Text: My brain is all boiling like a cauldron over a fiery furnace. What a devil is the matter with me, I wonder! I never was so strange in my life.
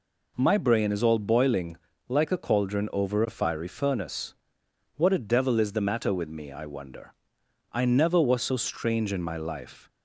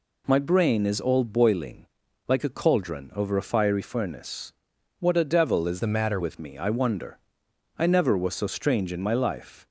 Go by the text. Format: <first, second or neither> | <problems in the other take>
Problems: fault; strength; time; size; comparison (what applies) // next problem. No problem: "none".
first | pauses between "boiling" and "like"; at 1.8 s; 0.42 s long; slight in the first // changes voice from "the" to "matter"; from 5.7 to 6.1 s; 0.4 s long